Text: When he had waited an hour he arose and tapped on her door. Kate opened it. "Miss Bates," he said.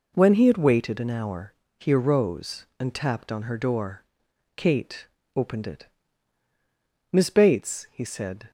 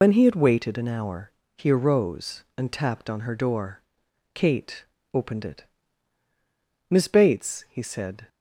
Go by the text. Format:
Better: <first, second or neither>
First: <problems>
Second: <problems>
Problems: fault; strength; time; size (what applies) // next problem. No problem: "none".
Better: first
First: pauses between "hour" and "he"; slight; at 1.5 s; 0.26 s long // pauses between "Kate" and "opened"; slight; at 5.0 s; 0.26 s long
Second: loses the start of "When"; at 0.0 s; 90 ms // pauses between "hour" and "he"; slight; at 1.3 s; 0.26 s long // pauses between "Kate" and "opened"; slight; at 4.8 s; 0.26 s long